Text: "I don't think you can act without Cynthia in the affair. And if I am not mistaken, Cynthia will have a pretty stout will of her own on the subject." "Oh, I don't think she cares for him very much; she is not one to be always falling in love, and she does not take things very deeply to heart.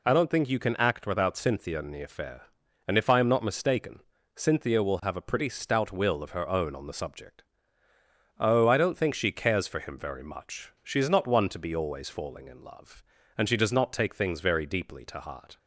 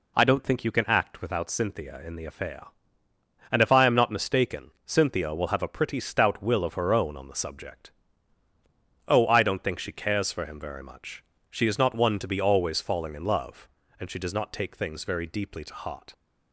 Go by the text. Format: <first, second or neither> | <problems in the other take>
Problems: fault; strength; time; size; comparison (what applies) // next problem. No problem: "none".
neither | none